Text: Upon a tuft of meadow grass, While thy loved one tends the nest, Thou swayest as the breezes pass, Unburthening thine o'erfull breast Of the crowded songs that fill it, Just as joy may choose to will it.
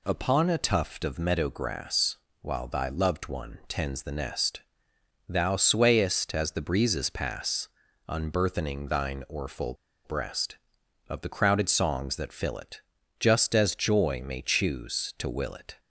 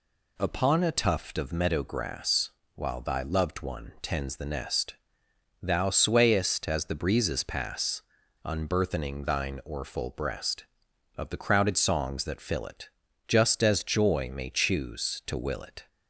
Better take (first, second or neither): second